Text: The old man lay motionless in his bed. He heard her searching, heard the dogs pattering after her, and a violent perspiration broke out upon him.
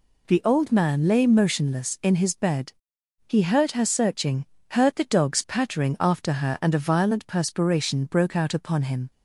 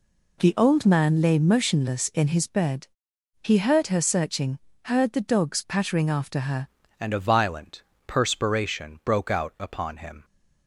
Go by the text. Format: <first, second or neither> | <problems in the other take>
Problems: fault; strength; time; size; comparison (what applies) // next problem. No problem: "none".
first | changes voice at "and"; from 6.9 s on; 3.3 s long // pauses between "violent" and "perspiration"; slight; at 7.8 s; 0.26 s long